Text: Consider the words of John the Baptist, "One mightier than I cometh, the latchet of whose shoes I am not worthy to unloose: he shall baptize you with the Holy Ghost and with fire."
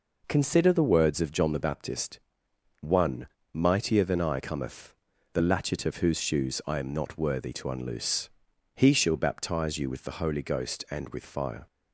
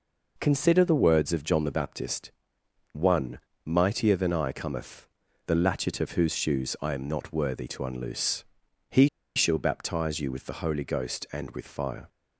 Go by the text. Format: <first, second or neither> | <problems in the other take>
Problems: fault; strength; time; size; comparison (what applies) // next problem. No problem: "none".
first | pauses between "One" and "mightier"; slight; at 3.3 s; 0.26 s long; slight in the first // pauses between "he" and "shall"; slight; at 9.0 s; 0.28 s long